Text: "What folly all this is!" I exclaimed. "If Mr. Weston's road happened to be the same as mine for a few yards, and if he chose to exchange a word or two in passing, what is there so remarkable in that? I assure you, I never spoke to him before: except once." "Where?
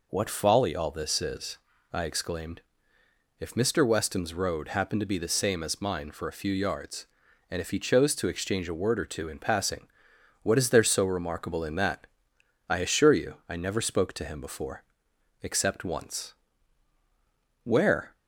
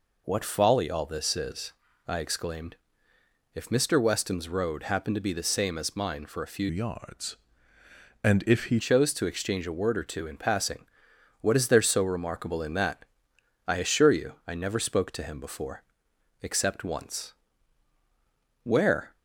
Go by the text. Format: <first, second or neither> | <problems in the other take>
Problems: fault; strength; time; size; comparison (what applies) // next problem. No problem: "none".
first | changes voice from "yards" to "he"; from 6.6 to 8.8 s; 2.2 s long